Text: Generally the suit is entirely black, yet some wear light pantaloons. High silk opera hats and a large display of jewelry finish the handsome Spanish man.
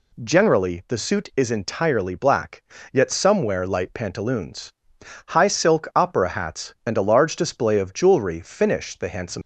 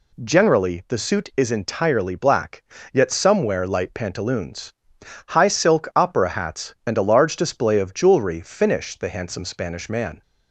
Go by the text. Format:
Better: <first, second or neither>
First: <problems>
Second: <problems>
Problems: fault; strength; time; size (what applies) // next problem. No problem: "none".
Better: second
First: stops before "Spanish man"; at 9.4 s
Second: none